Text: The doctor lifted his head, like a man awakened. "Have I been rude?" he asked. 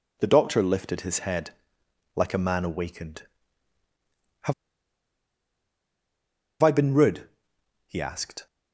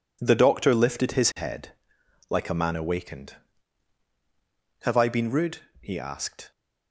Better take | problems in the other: second | pauses between "Have" and "I"; strong; at 4.5 s; 2.0 s long

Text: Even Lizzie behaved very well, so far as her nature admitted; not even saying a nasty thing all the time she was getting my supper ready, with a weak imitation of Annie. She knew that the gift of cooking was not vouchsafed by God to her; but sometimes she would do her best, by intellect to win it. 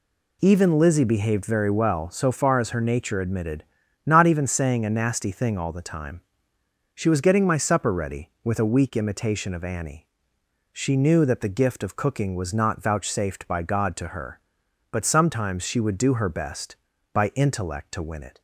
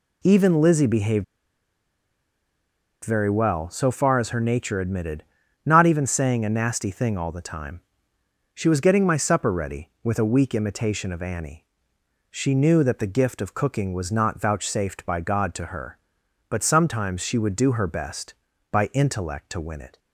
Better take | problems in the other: first | pauses between "behaved" and "very"; strong; at 1.2 s; 1.7 s long // pauses between "time" and "she"; noticeable; at 7.8 s; 0.74 s long; noticeable in the first

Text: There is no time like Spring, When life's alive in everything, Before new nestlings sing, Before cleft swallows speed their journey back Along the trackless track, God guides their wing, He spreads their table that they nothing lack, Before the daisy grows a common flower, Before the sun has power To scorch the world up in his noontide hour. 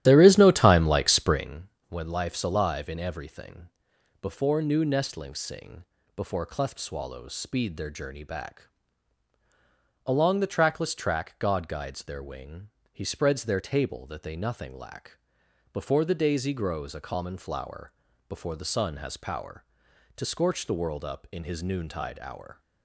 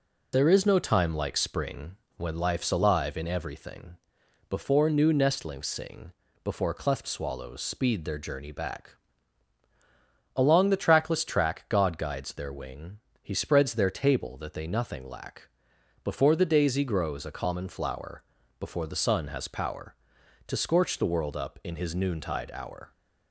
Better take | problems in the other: second | starts louder than the rest; strong; until 1.5 s; 13 dB // pauses between "back" and "Along"; strong; at 8.6 s; 1.3 s long; strong in the second

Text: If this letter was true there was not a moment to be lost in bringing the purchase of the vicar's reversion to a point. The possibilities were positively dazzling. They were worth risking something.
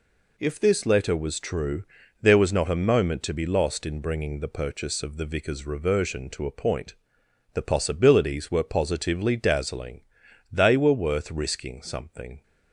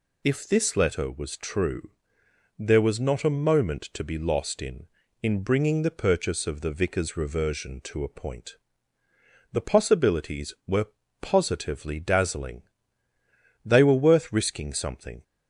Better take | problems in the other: first | pauses between "true" and "there"; noticeable; at 1.9 s; 0.70 s long; slight in the first // says "in" twice; at 5.2 s // pauses between "were" and "positively"; slight; at 10.8 s; 0.34 s long

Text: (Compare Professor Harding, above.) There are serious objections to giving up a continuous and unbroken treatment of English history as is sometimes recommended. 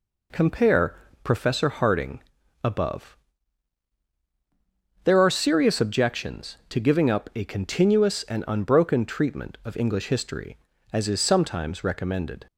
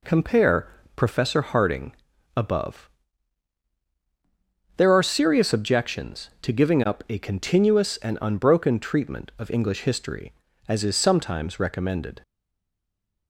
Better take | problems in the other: first | pauses between "Compare" and "Professor"; slight; at 0.6 s; 0.30 s long; slight in the first // stays silent after the last word; from 12.2 s on; 1.0 s long

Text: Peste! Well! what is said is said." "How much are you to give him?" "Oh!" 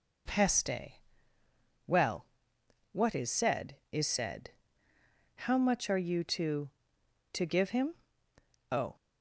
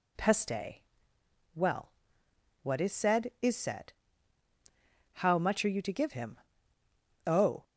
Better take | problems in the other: second | says "to" twice; at 7.3 s

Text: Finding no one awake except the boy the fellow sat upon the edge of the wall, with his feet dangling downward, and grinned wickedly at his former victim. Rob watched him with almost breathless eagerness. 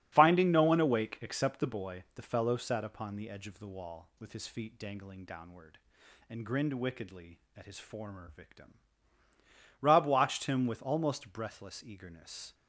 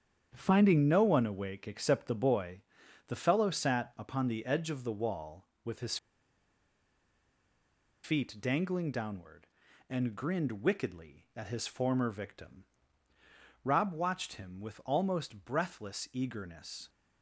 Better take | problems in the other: first | starts louder than the rest; strong; until 1.3 s; 8.5 dB; strong in the first // pauses between "boy" and "the"; noticeable; at 2.6 s; 0.48 s long // pauses between "his" and "feet"; strong; at 5.9 s; 2.0 s long

